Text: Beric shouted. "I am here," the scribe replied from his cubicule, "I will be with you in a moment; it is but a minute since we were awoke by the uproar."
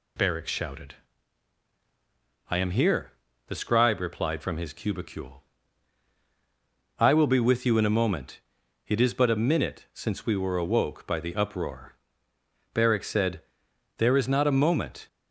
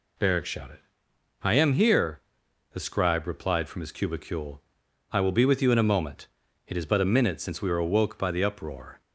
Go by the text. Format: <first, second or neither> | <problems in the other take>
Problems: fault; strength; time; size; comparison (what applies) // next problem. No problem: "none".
second | goes on to say "Beric said there is not a moment"; strong; from 12.7 s on; 2.3 s long